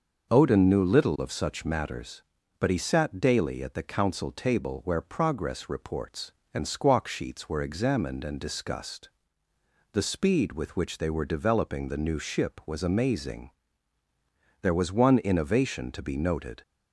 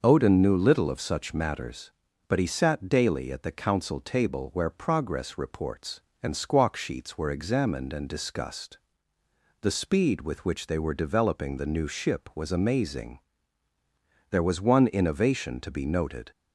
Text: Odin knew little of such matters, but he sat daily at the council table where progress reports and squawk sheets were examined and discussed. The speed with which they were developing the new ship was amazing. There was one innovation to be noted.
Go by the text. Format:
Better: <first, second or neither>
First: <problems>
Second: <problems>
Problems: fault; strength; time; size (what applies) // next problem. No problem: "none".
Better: neither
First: starts louder than the rest; noticeable; until 1.3 s; 6 dB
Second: starts louder than the rest; noticeable; until 1.0 s; 6 dB